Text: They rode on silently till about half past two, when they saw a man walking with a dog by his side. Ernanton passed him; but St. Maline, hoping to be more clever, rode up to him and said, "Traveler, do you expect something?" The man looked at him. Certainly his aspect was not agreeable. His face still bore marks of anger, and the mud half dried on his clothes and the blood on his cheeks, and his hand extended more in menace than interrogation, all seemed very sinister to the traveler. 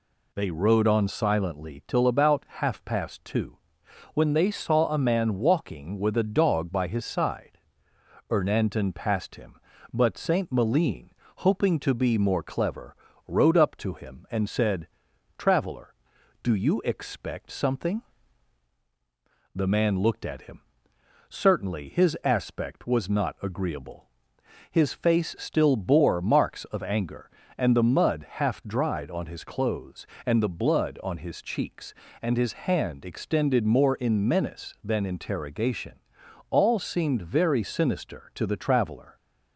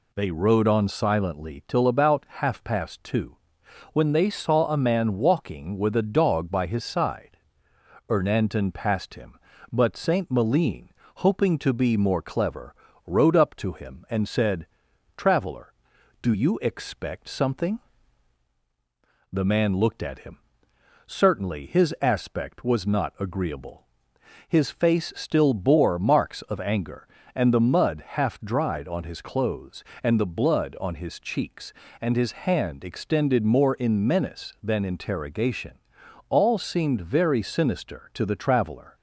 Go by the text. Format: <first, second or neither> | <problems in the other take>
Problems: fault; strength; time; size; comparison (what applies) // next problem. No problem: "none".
neither | none